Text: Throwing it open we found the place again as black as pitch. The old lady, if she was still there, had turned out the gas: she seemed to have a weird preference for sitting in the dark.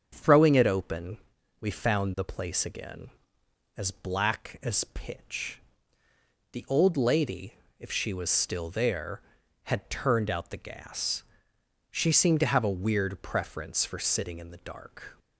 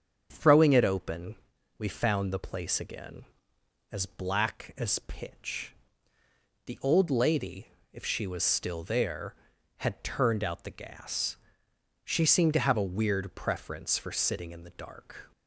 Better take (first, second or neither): neither